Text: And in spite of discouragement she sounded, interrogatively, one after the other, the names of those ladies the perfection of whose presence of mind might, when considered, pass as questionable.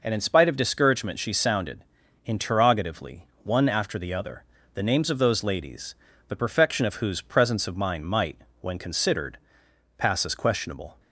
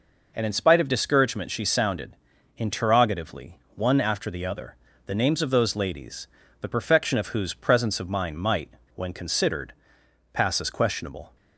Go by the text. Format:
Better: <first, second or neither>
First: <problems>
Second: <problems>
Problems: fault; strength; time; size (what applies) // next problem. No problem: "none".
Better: neither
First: pauses between "ladies" and "the"; slight; at 5.9 s; 0.34 s long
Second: pauses between "ladies" and "the"; slight; at 6.2 s; 0.34 s long